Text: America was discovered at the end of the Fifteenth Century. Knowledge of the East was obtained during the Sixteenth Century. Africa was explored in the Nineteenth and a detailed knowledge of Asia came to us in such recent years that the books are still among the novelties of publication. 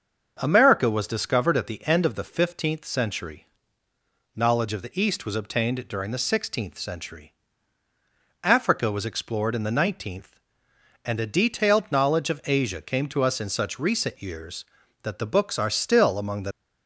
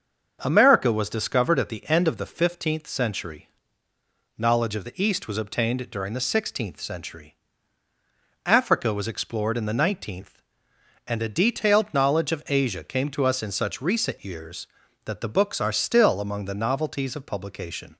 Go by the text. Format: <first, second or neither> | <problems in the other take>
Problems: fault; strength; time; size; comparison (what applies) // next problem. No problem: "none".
second | starts louder than the rest; until 1.4 s; 6.5 dB; also in the second // stops before "novelties of publication"; at 16.5 s